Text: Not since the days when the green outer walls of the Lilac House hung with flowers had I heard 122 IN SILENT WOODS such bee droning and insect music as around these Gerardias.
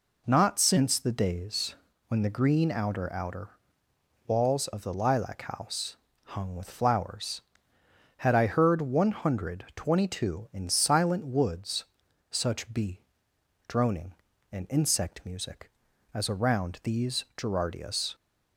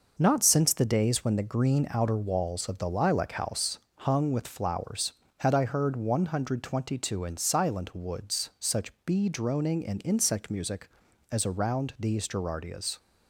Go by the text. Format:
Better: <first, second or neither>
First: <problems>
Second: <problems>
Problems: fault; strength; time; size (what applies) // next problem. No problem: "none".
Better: second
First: pauses between "days" and "when"; slight; at 1.7 s; 0.32 s long // says "outer" twice; at 3.1 s // pauses between "House" and "hung"; slight; at 5.9 s; 0.26 s long // pauses between "WOODS" and "such"; noticeable; at 11.8 s; 0.48 s long // pauses between "bee" and "droning"; noticeable; at 13.0 s; 0.66 s long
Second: pauses between "House" and "hung"; slight; at 3.7 s; 0.18 s long